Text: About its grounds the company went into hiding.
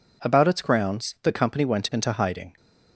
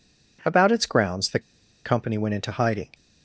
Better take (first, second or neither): first